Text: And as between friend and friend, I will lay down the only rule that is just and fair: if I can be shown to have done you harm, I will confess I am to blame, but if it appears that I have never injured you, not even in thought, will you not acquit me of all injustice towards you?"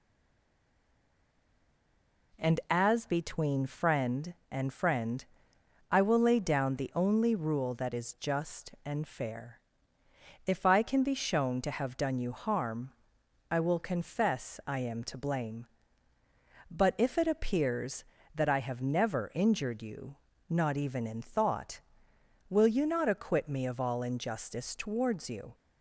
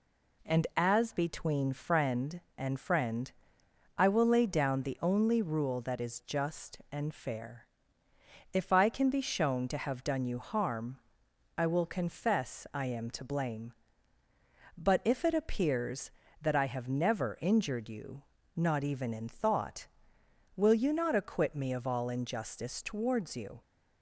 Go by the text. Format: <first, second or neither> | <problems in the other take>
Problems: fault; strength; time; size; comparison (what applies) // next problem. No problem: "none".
second | stays silent before the first word; until 2.3 s; 2.3 s long